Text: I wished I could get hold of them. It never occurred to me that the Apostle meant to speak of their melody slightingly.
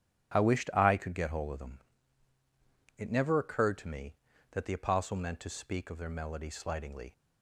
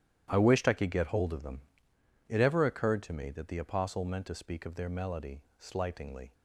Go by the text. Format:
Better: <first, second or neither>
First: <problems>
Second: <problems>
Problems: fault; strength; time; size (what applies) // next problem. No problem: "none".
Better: first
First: starts louder than the rest; strong; until 1.3 s; 11.5 dB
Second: starts louder than the rest; strong; until 1.3 s; 11 dB // says "ever" for "never"; at 2.3 s // pauses between "melody" and "slightingly"; slight; at 5.3 s; 0.18 s long